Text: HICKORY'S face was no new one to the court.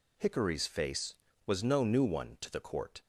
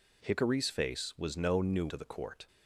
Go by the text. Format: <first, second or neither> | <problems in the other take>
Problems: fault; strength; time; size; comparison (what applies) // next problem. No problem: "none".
first | skips "one"; at 1.8 s